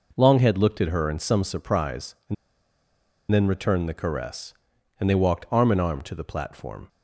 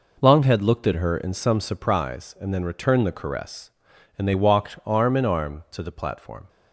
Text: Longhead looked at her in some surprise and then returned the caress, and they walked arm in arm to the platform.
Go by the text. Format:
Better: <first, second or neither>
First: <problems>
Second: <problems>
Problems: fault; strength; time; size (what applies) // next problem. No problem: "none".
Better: second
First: pauses between "and" and "then"; noticeable; at 2.3 s; 0.96 s long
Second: none